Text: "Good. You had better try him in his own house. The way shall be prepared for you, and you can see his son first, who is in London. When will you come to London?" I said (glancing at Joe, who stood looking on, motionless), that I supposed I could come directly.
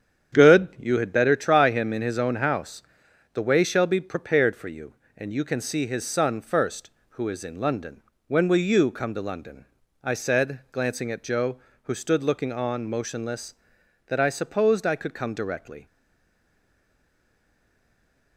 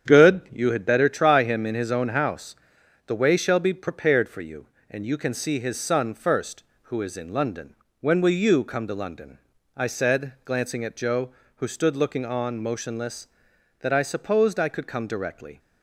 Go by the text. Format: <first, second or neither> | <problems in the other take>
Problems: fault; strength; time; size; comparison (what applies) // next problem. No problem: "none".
second | starts louder than the rest; strong; until 1.4 s; 8.5 dB; strong in the second // stays silent after the last word; strong; from 15.8 s on; 2.5 s long